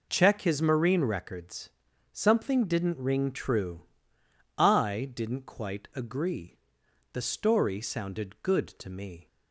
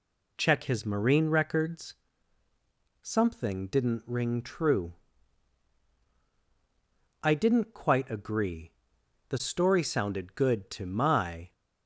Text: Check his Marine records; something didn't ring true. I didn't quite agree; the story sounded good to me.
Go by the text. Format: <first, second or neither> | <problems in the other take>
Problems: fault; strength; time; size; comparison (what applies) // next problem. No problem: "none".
first | says "my" for "me"; at 10.8 s